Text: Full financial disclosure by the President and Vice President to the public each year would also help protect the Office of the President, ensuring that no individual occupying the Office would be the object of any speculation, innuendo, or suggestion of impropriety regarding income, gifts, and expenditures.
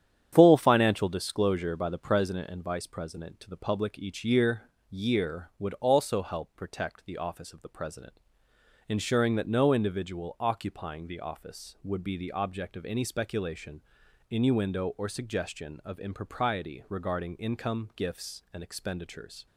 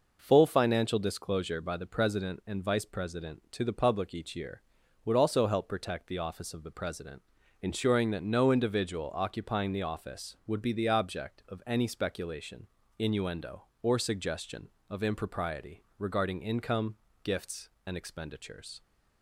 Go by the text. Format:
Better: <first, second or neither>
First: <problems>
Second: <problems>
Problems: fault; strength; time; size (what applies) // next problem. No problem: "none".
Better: second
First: starts louder than the rest; strong; until 1.3 s; 9.5 dB // says "year" twice; at 4.8 s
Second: none